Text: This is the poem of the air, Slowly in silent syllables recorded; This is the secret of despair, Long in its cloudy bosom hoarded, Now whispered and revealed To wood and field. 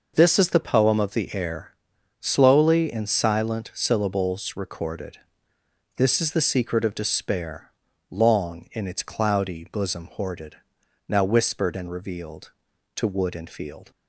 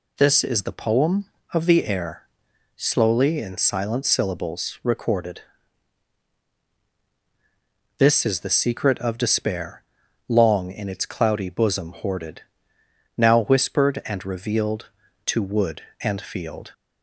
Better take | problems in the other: neither | none

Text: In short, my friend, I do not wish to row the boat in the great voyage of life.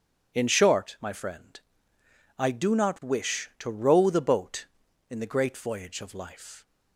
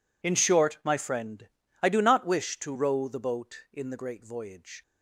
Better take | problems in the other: first | stops before "of life"; at 4.8 s

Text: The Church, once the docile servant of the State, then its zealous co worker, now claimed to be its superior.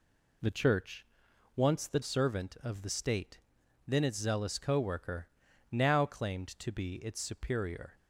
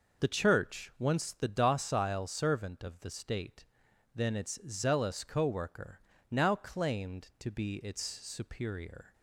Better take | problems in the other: second | skips "docile"; at 2.0 s

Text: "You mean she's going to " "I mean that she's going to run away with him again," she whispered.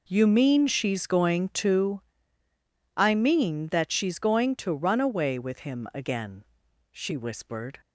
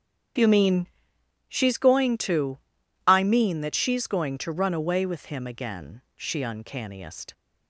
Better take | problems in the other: first | starts louder than the rest; strong; until 2.0 s; 8.5 dB // pauses between "mean" and "she's"; noticeable; at 0.8 s; 0.62 s long // says "uncanniest" for "whispered"; at 6.4 s

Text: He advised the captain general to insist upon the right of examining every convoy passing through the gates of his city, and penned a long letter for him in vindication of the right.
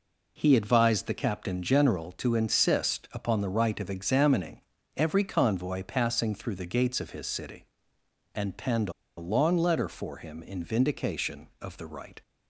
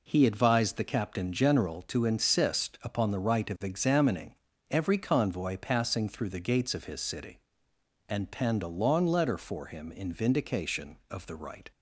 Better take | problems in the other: second | pauses between "examining" and "every"; slight; at 4.6 s; 0.34 s long; slight in the second // pauses between "penned" and "a"; slight; at 8.9 s; 0.26 s long

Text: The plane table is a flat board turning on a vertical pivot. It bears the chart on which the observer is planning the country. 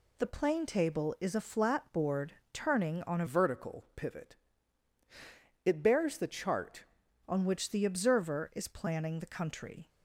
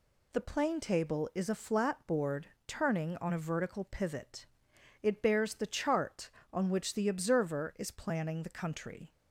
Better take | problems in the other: second | pauses between "board" and "turning"; slight; at 2.3 s; 0.18 s long; slight in the second // changes voice from "vertical" to "chart"; from 3.2 to 6.8 s; 3.6 s long

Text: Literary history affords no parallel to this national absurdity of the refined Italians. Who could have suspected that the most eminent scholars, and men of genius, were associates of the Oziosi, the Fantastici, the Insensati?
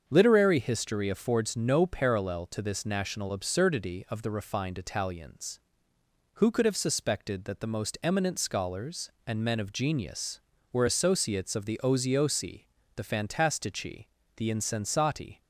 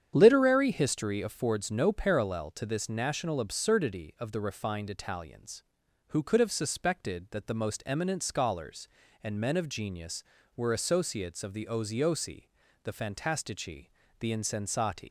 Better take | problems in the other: first | starts louder than the rest; strong; until 1.1 s; 8.5 dB; also in the first // leaves "Insensati" unfinished; at 15.0 s; 125 ms

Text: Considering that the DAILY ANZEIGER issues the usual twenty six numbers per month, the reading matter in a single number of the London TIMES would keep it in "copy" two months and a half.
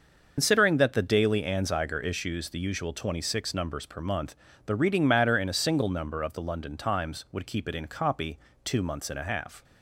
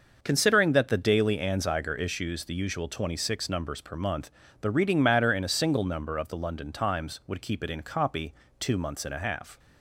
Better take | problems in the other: second | loses the start of "Considering"; at 0.3 s; 105 ms // starts louder than the rest; until 1.3 s; 6 dB; noticeable in the second // pauses between "copy" and "two"; slight; at 8.3 s; 0.26 s long; slight in the second

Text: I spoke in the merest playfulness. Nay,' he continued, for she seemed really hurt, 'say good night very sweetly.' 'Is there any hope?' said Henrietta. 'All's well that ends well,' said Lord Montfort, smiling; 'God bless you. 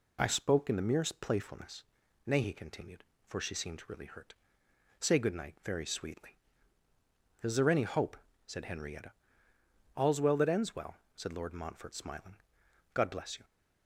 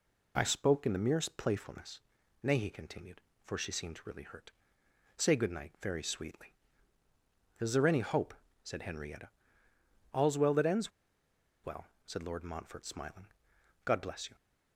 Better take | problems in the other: first | pauses between "ends" and "well"; noticeable; at 10.9 s; 0.74 s long

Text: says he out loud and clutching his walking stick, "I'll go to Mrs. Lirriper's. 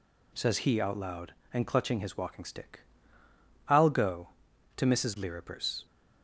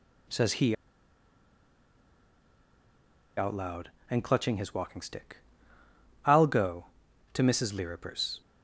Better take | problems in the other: first | pauses between "he" and "out"; strong; at 0.7 s; 2.6 s long

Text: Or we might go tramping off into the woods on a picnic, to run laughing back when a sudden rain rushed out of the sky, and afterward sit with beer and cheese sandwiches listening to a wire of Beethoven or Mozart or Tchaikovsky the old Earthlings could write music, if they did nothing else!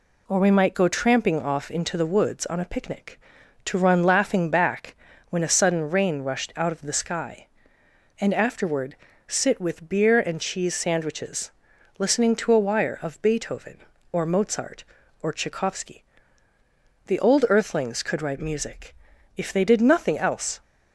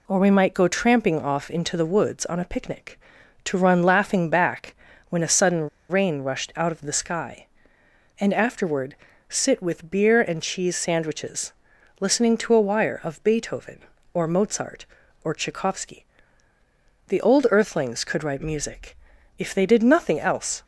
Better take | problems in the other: first | pauses between "back" and "when"; slight; at 4.7 s; 0.34 s long; slight in the first // pauses between "sudden" and "rain"; slight; at 5.6 s; 0.20 s long // pauses between "afterward" and "sit"; slight; at 8.9 s; 0.34 s long; slight in the first // pauses between "sandwiches" and "listening"; noticeable; at 11.5 s; 0.50 s long; noticeable in the first // pauses between "Tchaikovsky" and "the"; at 16.0 s; 1.0 s long; also in the first

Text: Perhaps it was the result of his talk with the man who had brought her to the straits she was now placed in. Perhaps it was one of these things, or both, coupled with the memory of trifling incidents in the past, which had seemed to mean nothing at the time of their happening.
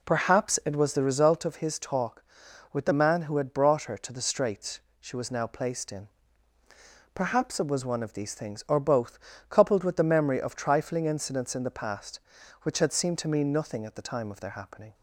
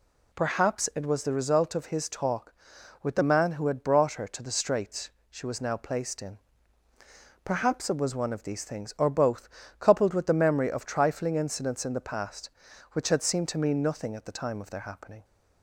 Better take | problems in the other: second | starts louder than the rest; slight; until 1.5 s; 3 dB // pauses between "straits" and "she"; slight; at 4.7 s; 0.20 s long; slight in the second

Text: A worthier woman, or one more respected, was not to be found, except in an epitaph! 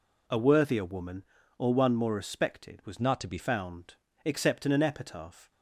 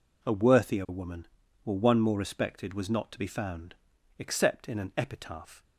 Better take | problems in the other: second | changes voice from "not" to "be"; from 2.9 to 3.3 s; 0.4 s long

